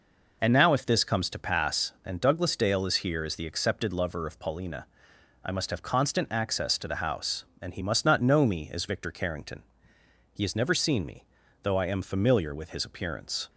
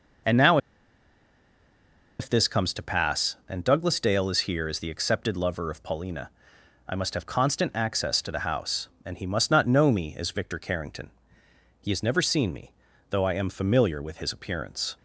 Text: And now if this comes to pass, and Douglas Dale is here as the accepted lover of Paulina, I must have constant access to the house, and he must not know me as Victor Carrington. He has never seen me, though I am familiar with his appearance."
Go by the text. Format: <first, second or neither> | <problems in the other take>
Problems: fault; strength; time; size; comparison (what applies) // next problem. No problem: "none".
first | pauses between "now" and "if"; strong; at 0.5 s; 1.6 s long